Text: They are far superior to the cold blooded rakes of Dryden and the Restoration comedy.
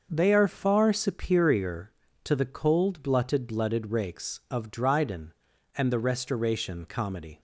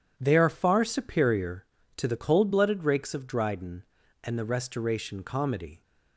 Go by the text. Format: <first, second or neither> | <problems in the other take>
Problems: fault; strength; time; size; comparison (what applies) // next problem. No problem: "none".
second | starts louder than the rest; until 1.1 s; 6 dB // says "blooded" twice; at 3.4 s